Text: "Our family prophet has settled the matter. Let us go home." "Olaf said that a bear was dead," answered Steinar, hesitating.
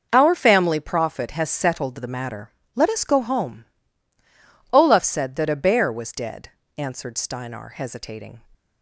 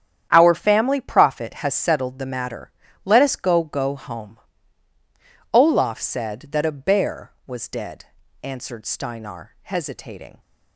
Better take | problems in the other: first | starts louder than the rest; strong; until 1.3 s; 9.5 dB // says "go" twice; at 3.6 s

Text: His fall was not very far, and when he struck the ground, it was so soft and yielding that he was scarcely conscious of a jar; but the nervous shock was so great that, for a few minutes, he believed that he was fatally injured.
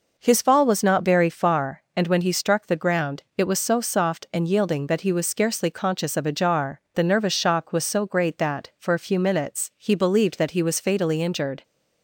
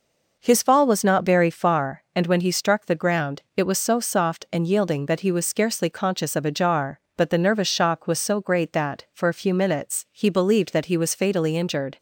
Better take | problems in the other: second | skips "but"; at 6.8 s

